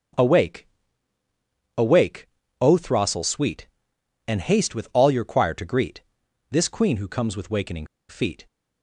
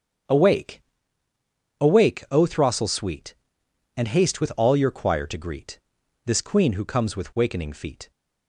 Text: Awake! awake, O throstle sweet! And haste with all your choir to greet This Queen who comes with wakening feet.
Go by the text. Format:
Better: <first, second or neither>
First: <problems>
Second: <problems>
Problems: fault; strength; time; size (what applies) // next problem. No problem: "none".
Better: second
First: starts louder than the rest; until 2.2 s; 6.5 dB // pauses between "greet" and "This"; noticeable; at 6.0 s; 0.50 s long // pauses between "wakening" and "feet"; slight; at 7.8 s; 0.22 s long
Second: starts louder than the rest; until 2.3 s; 7 dB // pauses between "greet" and "This"; noticeable; at 5.7 s; 0.48 s long